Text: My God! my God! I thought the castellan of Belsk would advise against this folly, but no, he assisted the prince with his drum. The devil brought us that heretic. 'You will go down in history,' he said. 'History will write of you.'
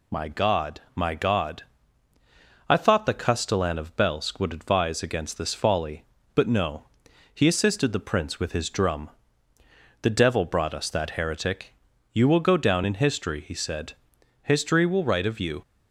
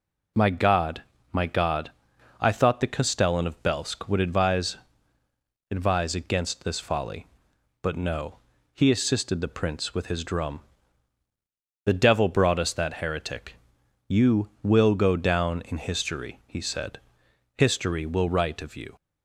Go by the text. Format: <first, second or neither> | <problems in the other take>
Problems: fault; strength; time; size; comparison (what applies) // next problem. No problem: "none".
first | says "advise" twice; at 5.6 s